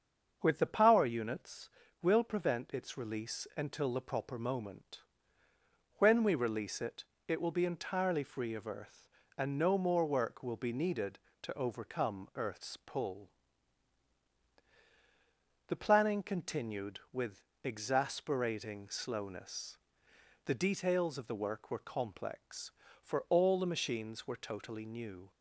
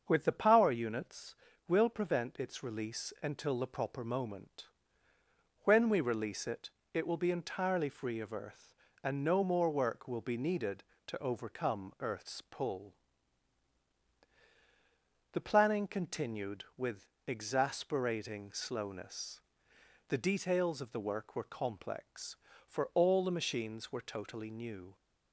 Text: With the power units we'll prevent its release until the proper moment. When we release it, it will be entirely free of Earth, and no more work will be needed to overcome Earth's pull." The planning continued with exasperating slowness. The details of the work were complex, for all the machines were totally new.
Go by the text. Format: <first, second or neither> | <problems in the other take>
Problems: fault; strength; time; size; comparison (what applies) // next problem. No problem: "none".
neither | starts louder than the rest; the same in both // pauses between "units" and "we'll"; slight; the same in both // pauses between "with" and "exasperating"; slight; the same in both